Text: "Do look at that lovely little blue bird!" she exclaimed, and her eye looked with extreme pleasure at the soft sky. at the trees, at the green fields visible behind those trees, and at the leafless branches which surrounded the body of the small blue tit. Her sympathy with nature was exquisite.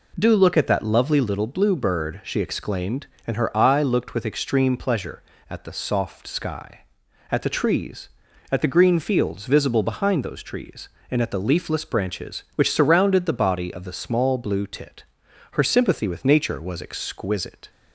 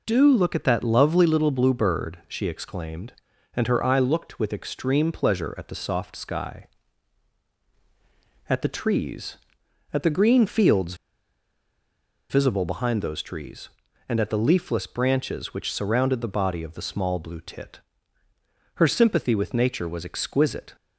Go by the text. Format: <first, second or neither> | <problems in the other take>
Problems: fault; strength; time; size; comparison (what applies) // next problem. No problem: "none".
first | pauses between "fields" and "visible"; strong; at 10.9 s; 1.3 s long